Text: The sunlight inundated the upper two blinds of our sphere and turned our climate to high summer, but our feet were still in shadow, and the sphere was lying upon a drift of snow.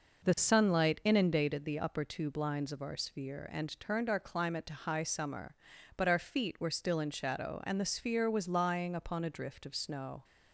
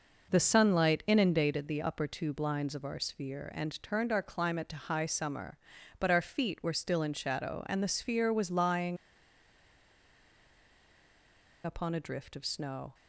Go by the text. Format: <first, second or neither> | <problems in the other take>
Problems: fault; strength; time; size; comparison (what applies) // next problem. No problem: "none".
first | pauses between "lying" and "upon"; strong; at 8.9 s; 2.6 s long